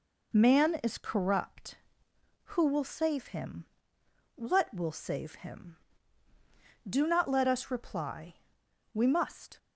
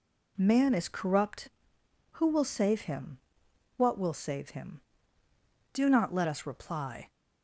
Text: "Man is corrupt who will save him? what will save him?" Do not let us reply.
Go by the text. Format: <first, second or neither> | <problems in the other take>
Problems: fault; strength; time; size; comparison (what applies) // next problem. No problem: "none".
second | goes on to say "We must"; noticeable; from 8.9 s on; 0.64 s long